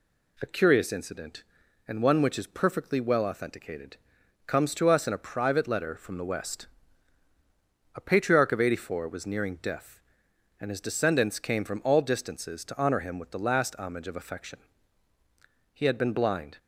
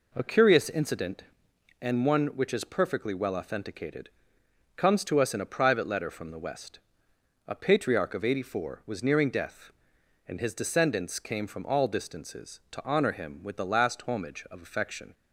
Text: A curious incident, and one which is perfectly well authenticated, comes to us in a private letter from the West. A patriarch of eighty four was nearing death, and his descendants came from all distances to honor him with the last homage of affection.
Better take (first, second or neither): second